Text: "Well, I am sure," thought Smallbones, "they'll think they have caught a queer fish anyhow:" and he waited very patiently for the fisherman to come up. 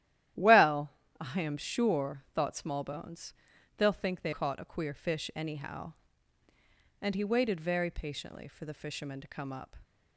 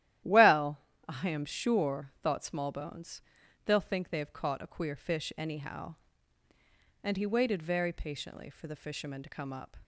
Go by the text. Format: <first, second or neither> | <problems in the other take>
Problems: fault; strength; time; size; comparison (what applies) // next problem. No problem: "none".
second | starts louder than the rest; strong; until 1.6 s; 12.5 dB; strong in the second // skips "have"; at 4.3 s